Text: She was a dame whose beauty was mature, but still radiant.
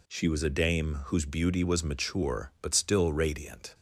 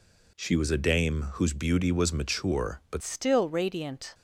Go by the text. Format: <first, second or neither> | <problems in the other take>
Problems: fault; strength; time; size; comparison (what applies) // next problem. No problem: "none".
first | changes voice at "still"; from 3.0 s on; 1.1 s long